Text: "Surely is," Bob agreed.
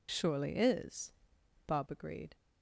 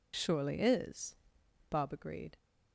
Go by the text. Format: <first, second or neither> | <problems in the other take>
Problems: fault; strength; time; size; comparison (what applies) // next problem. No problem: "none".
neither | none